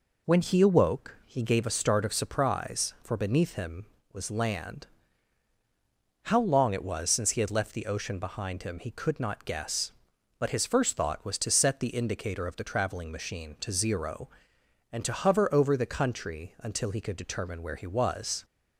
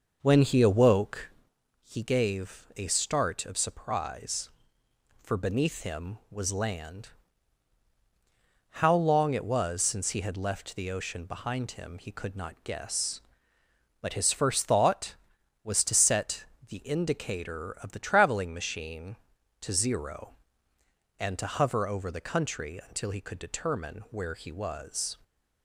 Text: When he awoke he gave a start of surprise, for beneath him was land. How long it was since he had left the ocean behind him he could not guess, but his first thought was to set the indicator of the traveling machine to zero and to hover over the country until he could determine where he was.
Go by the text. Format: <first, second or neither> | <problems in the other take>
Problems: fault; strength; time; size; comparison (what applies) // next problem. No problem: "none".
first | starts louder than the rest; noticeable; until 1.3 s; 6 dB // pauses between "awoke" and "he"; noticeable; at 1.2 s; 0.52 s long // pauses between "set" and "the"; slight; at 16.4 s; 0.24 s long